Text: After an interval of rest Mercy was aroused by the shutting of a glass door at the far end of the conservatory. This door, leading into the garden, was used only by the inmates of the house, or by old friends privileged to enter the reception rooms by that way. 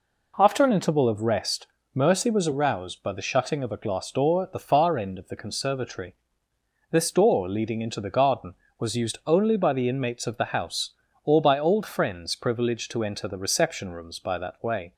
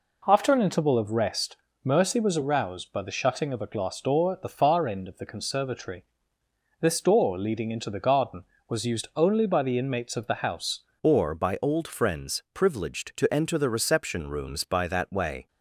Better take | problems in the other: first | pauses between "rest" and "Mercy"; slight; at 1.5 s; 0.26 s long; slight in the first // changes voice at "or"; from 11.0 s on; 4.4 s long

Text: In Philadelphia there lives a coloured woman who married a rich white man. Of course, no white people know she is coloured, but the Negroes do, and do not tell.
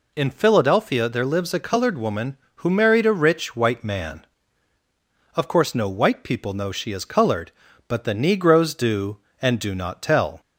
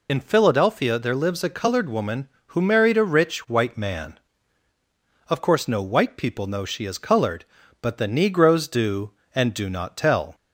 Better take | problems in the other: first | loses the start of "In"; at 0.0 s; 50 ms

